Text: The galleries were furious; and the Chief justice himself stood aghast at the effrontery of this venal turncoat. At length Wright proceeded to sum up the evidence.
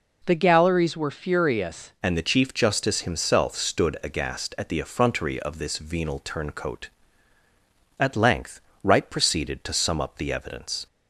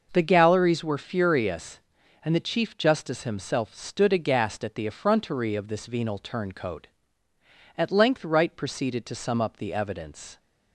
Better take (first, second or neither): second